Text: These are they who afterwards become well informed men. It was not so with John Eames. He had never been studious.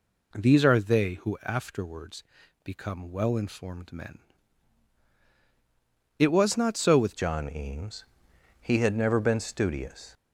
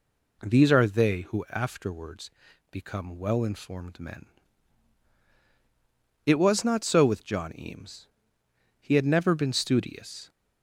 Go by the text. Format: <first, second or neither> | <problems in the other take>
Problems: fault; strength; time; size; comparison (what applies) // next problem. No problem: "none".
second | pauses between "afterwards" and "become"; at 2.2 s; 0.42 s long; also in the second // changes voice at "John"; from 7.1 s on; 3.0 s long